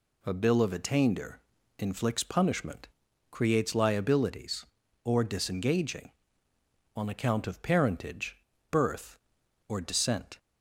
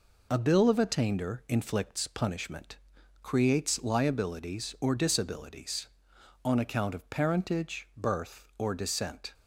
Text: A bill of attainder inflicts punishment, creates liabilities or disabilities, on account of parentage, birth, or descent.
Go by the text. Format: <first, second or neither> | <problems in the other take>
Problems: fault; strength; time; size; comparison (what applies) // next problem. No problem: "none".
second | pauses between "attainder" and "inflicts"; at 1.4 s; 0.38 s long // says "disengaging" for "disabilities"; at 5.2 s